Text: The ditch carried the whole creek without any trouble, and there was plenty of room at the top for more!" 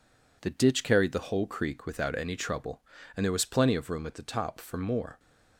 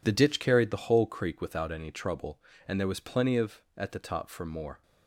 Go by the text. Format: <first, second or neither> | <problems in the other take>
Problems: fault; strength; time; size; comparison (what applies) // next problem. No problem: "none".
first | skips "room"; at 3.6 s